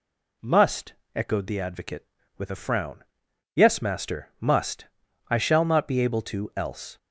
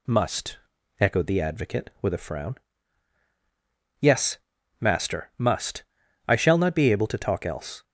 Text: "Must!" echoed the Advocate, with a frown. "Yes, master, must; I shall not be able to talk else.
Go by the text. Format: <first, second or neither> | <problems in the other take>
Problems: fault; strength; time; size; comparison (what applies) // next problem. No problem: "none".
second | skips "talk"; at 6.5 s